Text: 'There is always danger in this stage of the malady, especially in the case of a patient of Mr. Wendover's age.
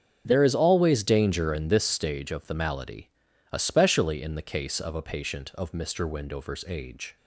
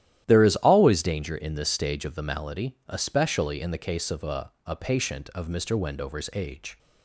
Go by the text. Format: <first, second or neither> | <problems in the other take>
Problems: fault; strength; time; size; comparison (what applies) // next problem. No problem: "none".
first | starts louder than the rest; strong; until 1.2 s; 12 dB; strong in the first // says "a" twice; at 4.6 s